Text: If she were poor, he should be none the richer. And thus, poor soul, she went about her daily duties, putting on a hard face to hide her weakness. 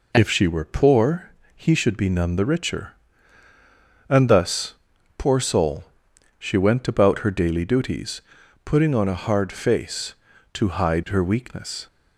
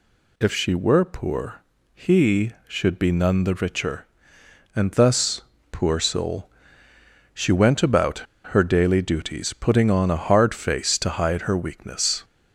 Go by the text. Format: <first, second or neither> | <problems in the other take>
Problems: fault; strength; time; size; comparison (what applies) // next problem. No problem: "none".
first | pauses between "about" and "her"; slight; at 8.1 s; 0.30 s long